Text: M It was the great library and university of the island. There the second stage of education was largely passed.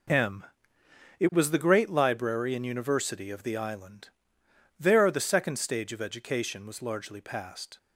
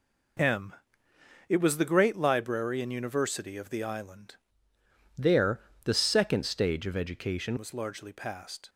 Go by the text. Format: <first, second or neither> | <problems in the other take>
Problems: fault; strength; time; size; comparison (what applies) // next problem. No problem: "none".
first | pauses between "M" and "It"; noticeable; at 0.7 s; 0.76 s long; noticeable in the first // changes voice from "There" to "education"; from 5.1 to 7.5 s; 2.4 s long // pauses between "There" and "the"; slight; at 5.5 s; 0.24 s long